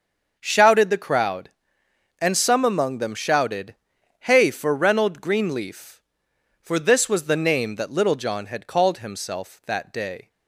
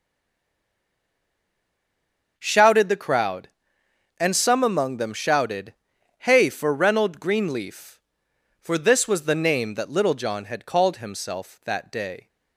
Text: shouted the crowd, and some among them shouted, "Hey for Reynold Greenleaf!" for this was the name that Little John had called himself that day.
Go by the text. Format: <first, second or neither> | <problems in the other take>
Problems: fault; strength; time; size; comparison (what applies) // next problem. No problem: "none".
first | stays silent before the first word; until 2.3 s; 2.3 s long // starts louder than the rest; until 3.3 s; 6.5 dB; also in the first